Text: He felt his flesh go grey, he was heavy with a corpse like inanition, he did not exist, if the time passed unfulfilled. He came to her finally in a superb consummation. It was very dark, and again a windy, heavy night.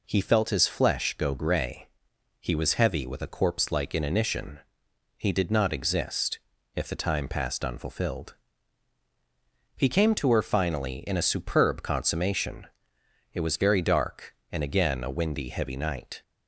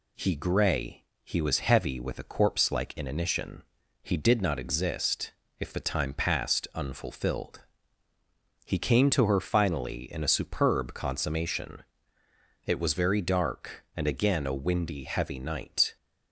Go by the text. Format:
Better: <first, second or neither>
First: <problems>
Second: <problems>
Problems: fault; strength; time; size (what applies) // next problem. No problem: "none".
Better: first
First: none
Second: skips "felt his flesh go"; at 0.3 s